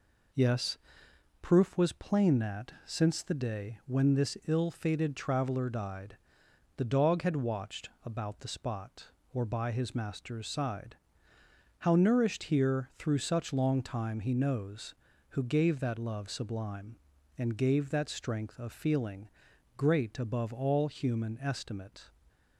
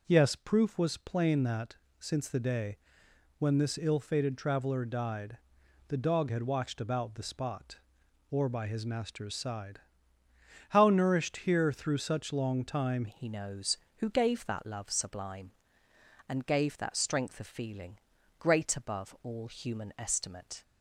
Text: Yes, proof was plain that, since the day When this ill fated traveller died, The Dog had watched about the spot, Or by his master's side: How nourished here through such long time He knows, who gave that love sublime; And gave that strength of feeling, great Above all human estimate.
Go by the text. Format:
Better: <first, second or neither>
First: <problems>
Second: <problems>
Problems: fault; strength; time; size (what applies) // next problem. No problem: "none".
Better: first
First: none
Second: pauses between "day" and "When"; noticeable; at 2.7 s; 0.62 s long // changes voice at "He"; from 13.0 s on; 7.6 s long